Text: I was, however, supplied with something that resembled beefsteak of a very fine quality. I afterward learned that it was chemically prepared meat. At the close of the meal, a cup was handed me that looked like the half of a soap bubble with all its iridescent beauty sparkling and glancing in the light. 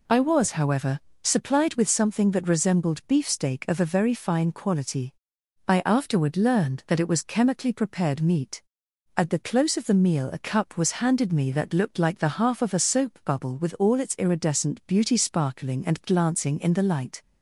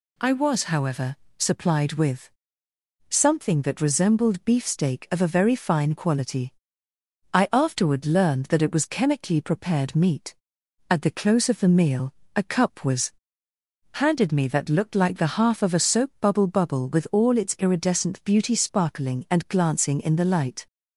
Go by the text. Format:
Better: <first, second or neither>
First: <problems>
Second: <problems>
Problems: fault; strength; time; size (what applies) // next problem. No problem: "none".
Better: first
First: none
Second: pauses between "with" and "something"; noticeable; at 2.3 s; 0.80 s long // pauses between "was" and "handed"; noticeable; at 13.1 s; 0.80 s long // says "bubble" twice; at 16.4 s